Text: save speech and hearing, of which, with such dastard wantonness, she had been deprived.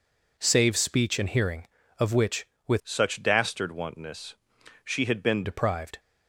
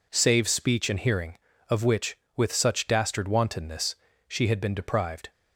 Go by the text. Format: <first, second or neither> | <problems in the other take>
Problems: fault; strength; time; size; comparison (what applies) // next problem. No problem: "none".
second | changes voice from "such" to "been"; from 2.8 to 5.4 s; 2.6 s long